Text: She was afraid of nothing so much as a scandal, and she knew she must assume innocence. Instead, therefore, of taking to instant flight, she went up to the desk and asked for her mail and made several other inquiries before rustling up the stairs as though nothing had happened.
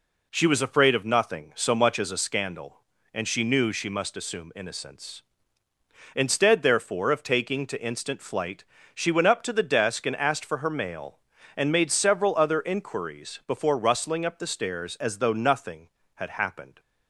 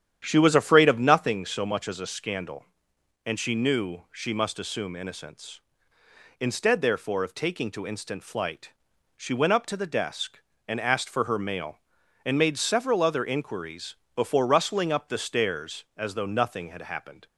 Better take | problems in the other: first | starts louder than the rest; strong; until 1.4 s; 9.5 dB // pauses between "inquiries" and "before"; slight; at 13.9 s; 0.18 s long

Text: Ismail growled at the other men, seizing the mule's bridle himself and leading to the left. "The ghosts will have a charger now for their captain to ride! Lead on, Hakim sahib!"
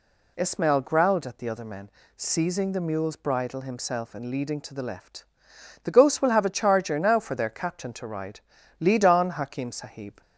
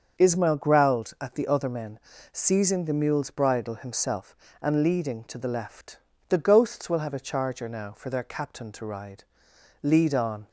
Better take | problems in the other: first | starts louder than the rest; until 1.2 s; 6.5 dB // stops before "Hakim sahib"; at 10.4 s

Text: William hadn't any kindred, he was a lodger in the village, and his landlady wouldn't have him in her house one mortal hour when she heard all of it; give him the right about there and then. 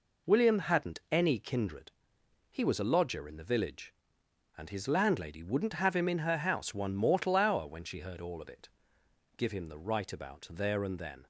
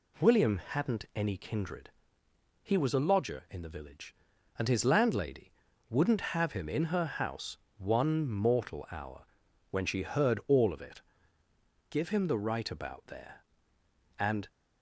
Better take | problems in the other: first | pauses between "landlady" and "wouldn't"; at 5.5 s; 0.38 s long // pauses between "house" and "one"; slight; at 7.5 s; 0.20 s long // pauses between "hour" and "when"; noticeable; at 9.2 s; 0.46 s long // stops before "then"; at 14.4 s

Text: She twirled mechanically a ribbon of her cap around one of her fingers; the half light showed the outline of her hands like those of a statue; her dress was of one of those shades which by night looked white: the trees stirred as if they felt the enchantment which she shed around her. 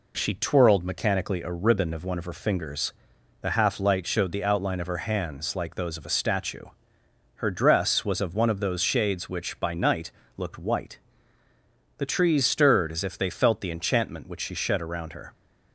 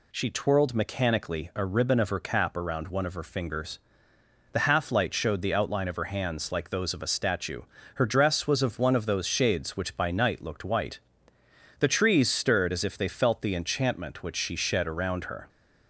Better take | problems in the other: second | skips "her cap around"; at 2.0 s // pauses between "night" and "looked"; slight; at 10.1 s; 0.26 s long

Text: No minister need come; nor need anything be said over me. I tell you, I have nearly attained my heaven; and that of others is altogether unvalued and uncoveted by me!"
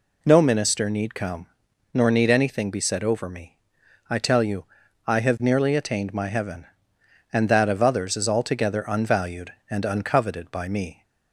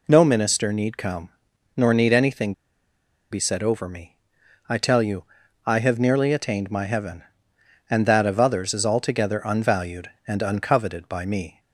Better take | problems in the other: first | pauses between "anything" and "be"; noticeable; at 2.5 s; 0.79 s long

